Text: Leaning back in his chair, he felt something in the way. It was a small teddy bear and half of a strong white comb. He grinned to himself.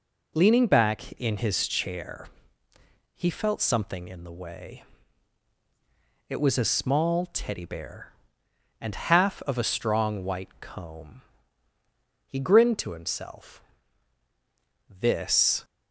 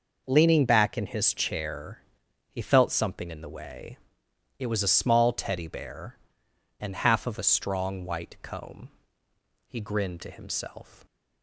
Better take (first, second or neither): second